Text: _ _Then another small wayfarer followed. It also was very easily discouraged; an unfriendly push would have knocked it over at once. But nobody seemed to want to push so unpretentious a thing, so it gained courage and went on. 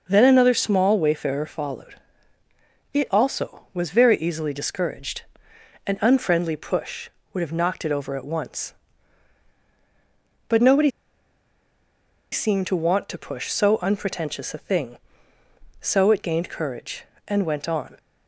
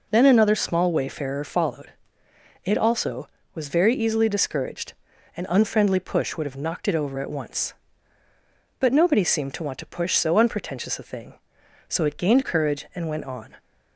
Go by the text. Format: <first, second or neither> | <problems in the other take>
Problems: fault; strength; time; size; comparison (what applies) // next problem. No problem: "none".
second | pauses between "nobody" and "seemed"; strong; at 10.8 s; 1.4 s long